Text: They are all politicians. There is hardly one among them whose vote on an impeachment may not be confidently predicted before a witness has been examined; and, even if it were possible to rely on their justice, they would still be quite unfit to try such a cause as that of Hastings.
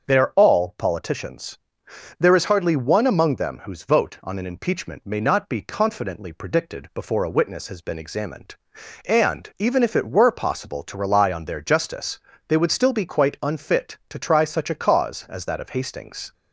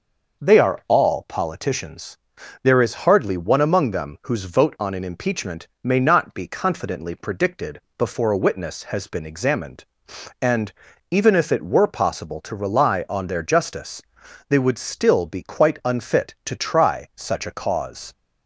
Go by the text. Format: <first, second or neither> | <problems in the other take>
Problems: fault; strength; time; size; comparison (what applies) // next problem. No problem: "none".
first | starts louder than the rest; noticeable; until 1.5 s; 6 dB; also in the first // pauses between "impeachment" and "may"; slight; at 5.6 s; 0.16 s long // pauses between "predicted" and "before"; slight; at 7.7 s; 0.16 s long // stops before "as that of Hastings"; at 18.1 s